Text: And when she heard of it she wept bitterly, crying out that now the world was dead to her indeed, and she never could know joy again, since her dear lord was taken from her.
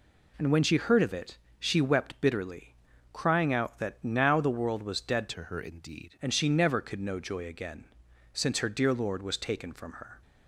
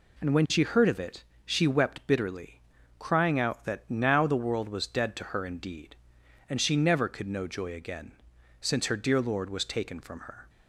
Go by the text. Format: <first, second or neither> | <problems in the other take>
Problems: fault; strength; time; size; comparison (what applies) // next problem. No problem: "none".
second | pauses between "it" and "she"; slight; at 1.3 s; 0.22 s long; slight in the second // changes voice from "to" to "indeed"; from 5.2 to 6.1 s; 0.9 s long